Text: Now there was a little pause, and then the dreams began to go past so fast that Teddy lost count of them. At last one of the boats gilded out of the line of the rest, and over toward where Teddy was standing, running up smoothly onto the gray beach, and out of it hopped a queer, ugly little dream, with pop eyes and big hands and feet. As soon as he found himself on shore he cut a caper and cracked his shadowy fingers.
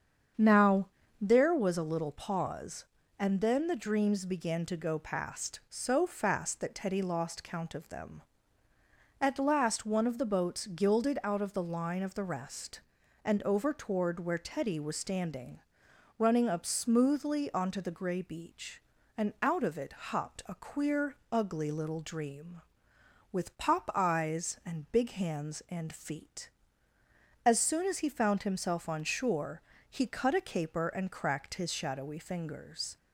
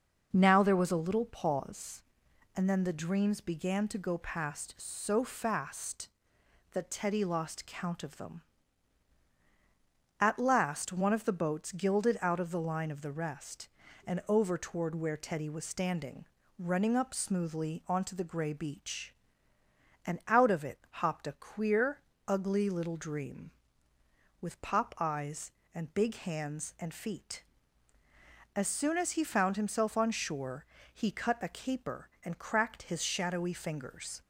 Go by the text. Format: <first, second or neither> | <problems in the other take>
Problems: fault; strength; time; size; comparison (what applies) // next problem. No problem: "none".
second | starts louder than the rest; strong; until 1.3 s; 7.5 dB // pauses between "Now" and "there"; slight; at 0.8 s; 0.32 s long // pauses between "shore" and "he"; slight; at 29.6 s; 0.28 s long; slight in the second